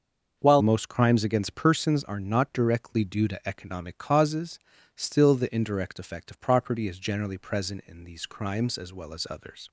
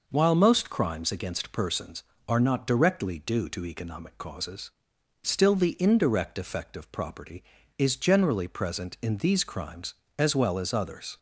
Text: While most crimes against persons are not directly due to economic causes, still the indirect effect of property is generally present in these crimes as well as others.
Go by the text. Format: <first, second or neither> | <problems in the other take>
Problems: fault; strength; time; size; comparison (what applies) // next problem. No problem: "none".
second | starts louder than the rest; until 1.4 s; 6 dB // changes voice at "most"; from 0.5 s on; 9.1 s long